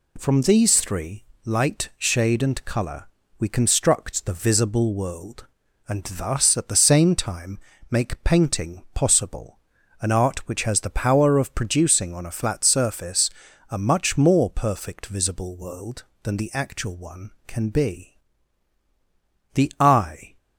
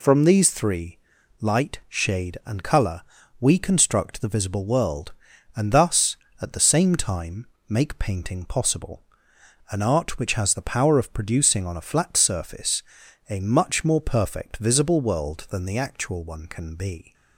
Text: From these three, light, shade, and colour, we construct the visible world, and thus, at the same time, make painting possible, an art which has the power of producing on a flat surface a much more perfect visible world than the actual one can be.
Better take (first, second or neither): second